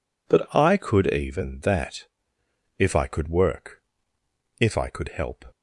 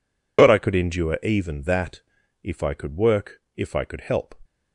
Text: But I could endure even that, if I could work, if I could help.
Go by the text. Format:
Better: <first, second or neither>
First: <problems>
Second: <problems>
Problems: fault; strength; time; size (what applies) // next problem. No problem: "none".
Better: second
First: skips "endure"; at 1.0 s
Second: none